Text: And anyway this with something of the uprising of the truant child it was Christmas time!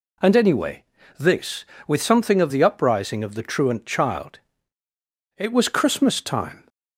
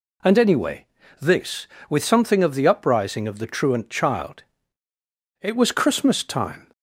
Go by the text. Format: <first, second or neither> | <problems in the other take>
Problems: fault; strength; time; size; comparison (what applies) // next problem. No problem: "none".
neither | pauses between "anyway" and "this"; slight; the same in both // pauses between "child" and "it"; the same in both